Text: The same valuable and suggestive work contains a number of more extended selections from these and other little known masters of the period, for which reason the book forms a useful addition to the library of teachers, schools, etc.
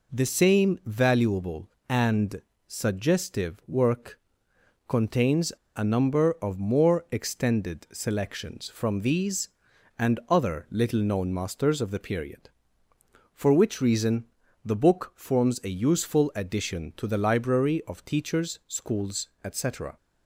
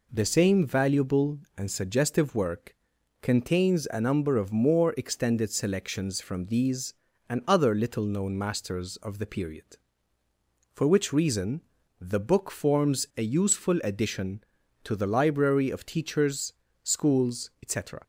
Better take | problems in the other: second | pauses between "and" and "suggestive"; slight; at 2.4 s; 0.24 s long // pauses between "work" and "contains"; noticeable; at 4.1 s; 0.70 s long; noticeable in the second // pauses between "contains" and "a"; slight; at 5.5 s; 0.25 s long // pauses between "reason" and "the"; at 14.2 s; 0.40 s long; also in the second

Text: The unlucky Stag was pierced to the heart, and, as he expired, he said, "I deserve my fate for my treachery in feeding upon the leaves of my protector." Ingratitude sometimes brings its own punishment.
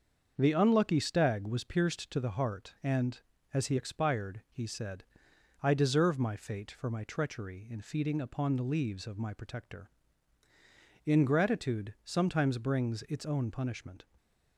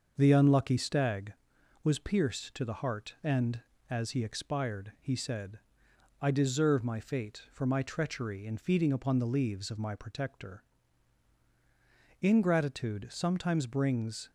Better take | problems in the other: first | starts louder than the rest; until 1.1 s; 6.5 dB; also in the first // stops before "its own punishment"; at 14.2 s

